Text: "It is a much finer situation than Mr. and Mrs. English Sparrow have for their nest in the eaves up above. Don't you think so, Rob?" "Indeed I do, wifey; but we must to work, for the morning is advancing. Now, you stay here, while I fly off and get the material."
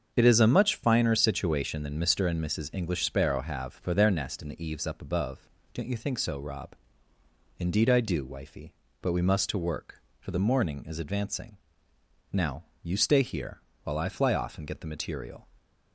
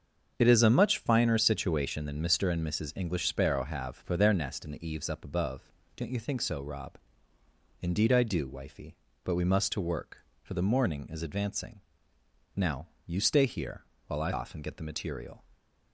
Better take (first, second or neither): first